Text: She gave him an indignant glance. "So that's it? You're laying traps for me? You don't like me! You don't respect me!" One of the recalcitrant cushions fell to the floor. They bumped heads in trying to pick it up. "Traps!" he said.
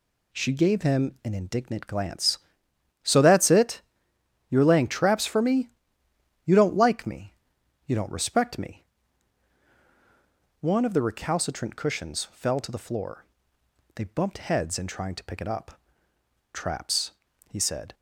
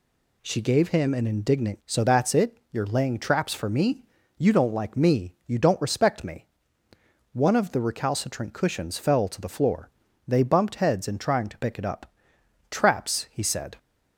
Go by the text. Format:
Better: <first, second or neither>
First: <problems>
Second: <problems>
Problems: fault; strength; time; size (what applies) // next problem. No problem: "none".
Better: first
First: none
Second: skips "glance"; at 1.8 s